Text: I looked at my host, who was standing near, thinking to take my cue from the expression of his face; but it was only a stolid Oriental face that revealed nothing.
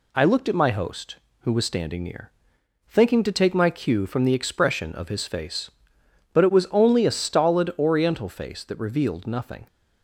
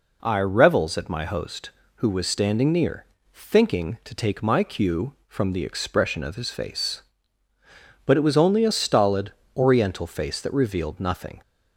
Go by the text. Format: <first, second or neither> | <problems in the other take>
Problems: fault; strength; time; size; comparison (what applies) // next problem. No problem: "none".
first | says "revels" for "looked"; at 0.3 s // pauses between "stolid" and "Oriental"; slight; at 9.3 s; 0.24 s long